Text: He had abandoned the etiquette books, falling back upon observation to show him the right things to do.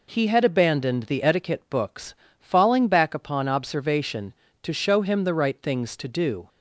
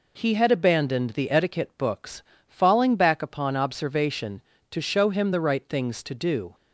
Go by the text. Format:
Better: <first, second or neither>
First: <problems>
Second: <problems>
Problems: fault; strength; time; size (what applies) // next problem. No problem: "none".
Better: neither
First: none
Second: none